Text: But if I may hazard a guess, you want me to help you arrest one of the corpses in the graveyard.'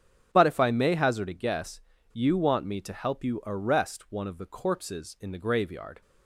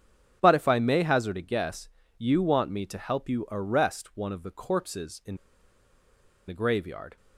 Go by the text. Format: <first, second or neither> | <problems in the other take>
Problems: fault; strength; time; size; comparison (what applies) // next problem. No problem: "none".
first | starts louder than the rest; strong; until 1.4 s; 8.5 dB; strong in the first // pauses between "in" and "the"; at 5.3 s; 1.1 s long